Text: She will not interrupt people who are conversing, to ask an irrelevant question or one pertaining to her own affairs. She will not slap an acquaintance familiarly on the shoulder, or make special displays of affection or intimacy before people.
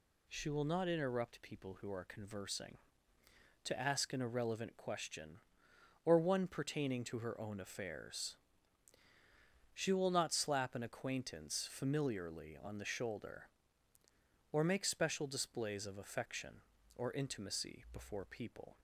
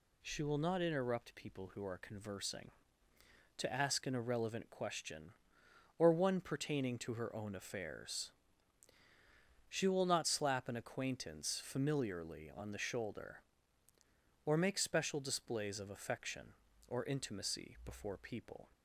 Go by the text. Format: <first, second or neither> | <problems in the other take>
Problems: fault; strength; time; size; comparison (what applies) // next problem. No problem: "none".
neither | none